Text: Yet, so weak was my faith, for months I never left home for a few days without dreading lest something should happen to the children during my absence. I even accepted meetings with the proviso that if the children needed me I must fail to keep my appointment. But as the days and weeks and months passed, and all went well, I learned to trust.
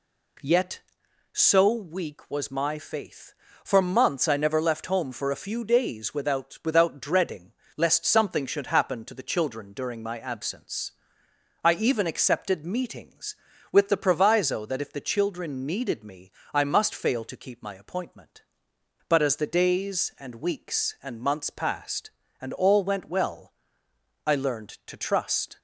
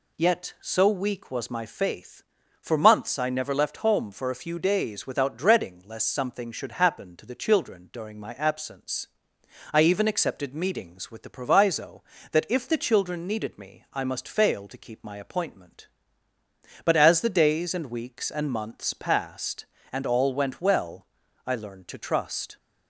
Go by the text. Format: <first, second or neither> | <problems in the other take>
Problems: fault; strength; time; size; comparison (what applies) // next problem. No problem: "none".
second | says "without" twice; at 6.6 s // pauses between "dreading" and "lest"; slight; at 7.5 s; 0.24 s long // pauses between "me" and "I"; slight; at 16.3 s; 0.22 s long